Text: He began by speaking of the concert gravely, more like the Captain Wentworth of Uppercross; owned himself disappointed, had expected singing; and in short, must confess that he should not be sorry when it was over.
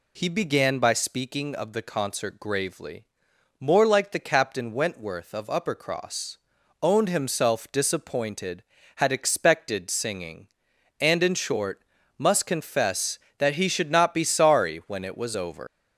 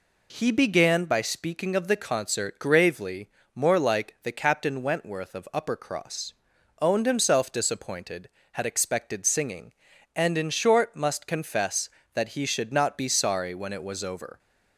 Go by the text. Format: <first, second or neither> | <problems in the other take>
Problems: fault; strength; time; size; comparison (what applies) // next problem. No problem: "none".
second | leaves "over" unfinished; at 15.6 s; 130 ms